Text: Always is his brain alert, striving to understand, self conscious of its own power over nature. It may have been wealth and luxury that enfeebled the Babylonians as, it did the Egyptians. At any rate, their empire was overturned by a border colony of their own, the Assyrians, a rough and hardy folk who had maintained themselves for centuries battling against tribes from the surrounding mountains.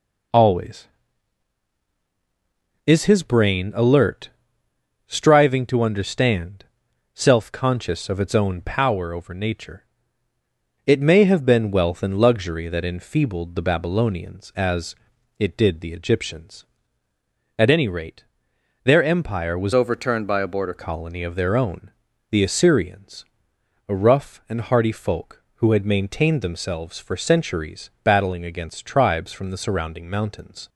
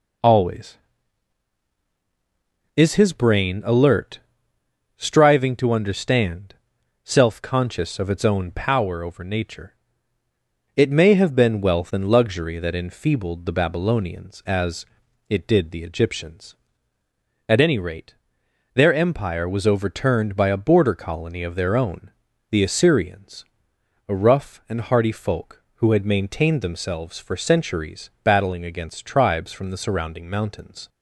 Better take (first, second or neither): second